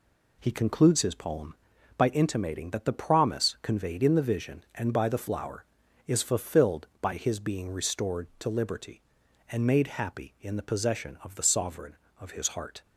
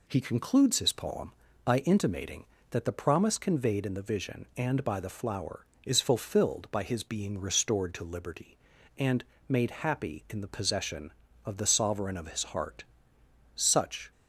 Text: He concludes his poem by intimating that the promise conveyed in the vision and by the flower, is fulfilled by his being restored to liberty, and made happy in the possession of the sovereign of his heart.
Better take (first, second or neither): first